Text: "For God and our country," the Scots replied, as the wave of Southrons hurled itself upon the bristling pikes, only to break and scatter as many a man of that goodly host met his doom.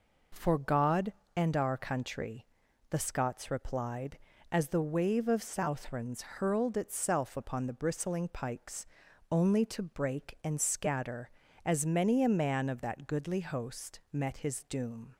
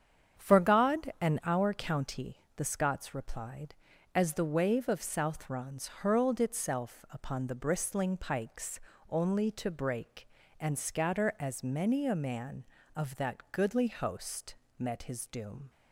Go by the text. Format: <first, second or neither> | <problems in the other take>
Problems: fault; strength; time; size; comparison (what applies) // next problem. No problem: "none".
first | starts louder than the rest; strong; until 1.5 s; 8 dB // says "county" for "country"; at 1.7 s // pauses between "host" and "met"; slight; at 14.5 s; 0.24 s long